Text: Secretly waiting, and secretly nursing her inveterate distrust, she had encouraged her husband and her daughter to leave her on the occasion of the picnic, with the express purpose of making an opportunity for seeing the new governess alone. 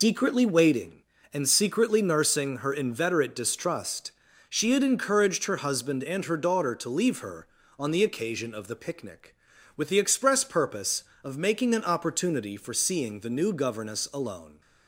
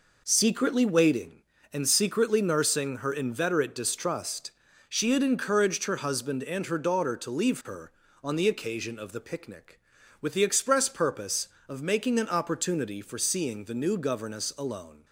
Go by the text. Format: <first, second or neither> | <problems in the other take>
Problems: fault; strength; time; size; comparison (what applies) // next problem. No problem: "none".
second | loses the start of "Secretly"; at 0.0 s; 150 ms